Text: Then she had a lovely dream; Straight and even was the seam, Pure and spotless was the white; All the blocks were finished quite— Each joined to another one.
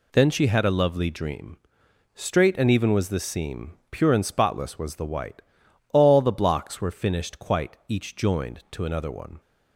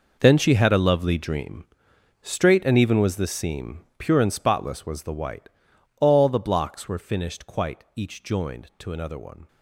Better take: first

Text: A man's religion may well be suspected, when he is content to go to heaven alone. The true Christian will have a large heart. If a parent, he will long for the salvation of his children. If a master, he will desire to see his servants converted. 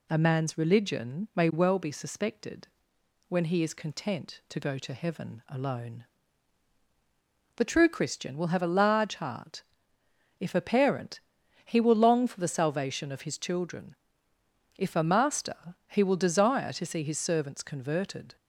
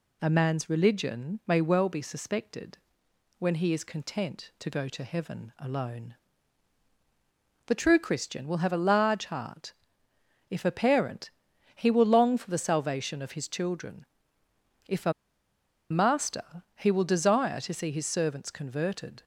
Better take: first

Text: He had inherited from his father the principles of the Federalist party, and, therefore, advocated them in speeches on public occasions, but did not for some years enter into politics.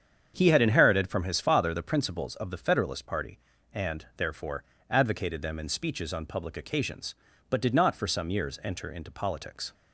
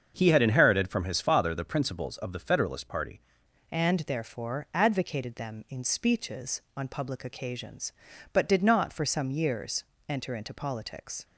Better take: first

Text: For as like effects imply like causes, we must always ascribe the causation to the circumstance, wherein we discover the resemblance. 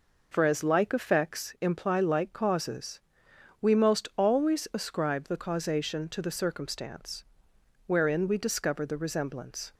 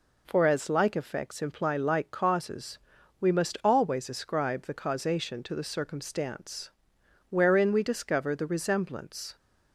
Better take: second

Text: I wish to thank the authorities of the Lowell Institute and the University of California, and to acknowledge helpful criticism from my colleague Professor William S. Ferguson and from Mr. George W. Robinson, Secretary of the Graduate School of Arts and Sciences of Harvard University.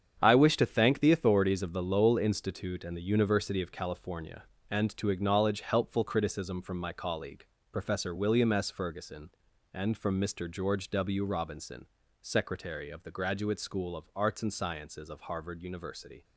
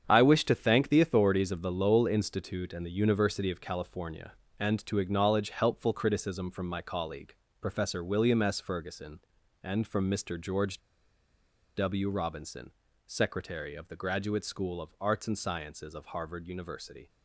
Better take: first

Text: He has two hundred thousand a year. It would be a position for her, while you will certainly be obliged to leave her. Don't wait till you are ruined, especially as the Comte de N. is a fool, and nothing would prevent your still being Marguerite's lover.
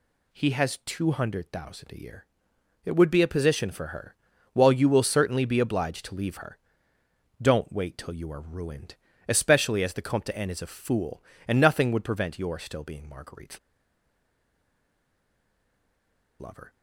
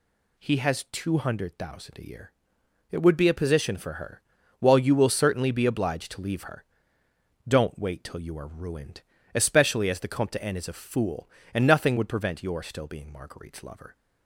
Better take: second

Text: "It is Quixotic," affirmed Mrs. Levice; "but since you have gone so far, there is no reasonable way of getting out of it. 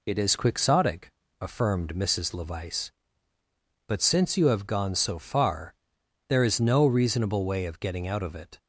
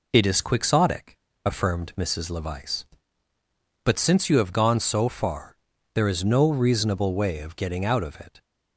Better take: neither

